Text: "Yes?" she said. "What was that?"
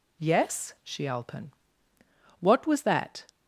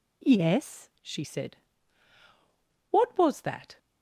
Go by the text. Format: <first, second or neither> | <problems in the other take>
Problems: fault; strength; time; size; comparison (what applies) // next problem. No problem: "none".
second | says "alpen" for "said"; at 1.0 s